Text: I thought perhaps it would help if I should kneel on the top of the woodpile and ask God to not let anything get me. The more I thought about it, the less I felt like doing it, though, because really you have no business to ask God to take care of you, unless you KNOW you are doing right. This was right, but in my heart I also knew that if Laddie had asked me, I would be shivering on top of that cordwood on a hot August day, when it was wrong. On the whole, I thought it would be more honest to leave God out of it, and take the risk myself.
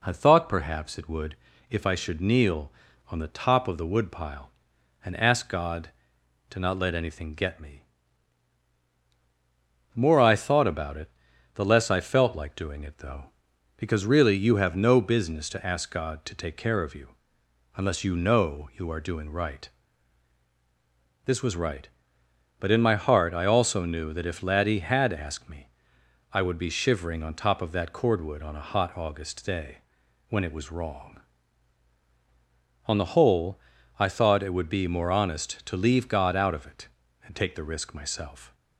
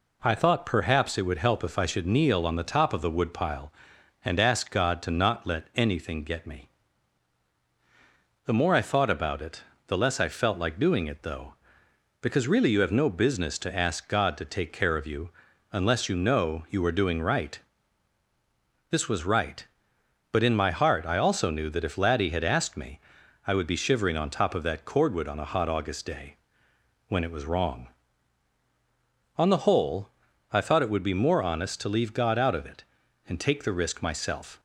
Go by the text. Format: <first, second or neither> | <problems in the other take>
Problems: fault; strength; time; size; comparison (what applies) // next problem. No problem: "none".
second | skips "help"; at 1.5 s